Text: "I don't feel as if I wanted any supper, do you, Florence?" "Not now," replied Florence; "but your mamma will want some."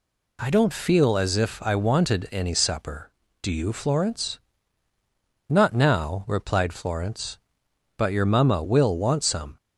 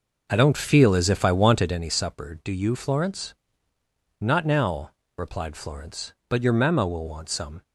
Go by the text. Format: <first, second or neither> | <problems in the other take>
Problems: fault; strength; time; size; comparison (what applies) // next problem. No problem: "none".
first | starts louder than the rest; noticeable; until 1.9 s; 5.5 dB